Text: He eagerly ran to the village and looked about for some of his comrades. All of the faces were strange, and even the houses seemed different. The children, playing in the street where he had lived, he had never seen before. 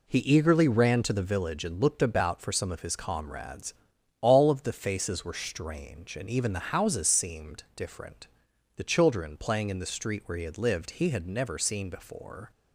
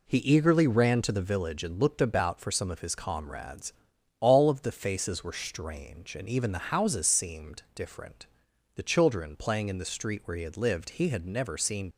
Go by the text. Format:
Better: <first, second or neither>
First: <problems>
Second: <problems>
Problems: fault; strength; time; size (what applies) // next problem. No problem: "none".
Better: first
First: none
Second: stops before "before"; at 11.9 s